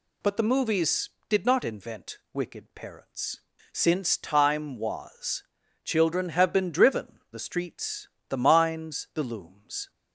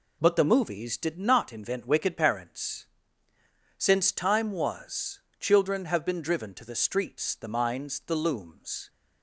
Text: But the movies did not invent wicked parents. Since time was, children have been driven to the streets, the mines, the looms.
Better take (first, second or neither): second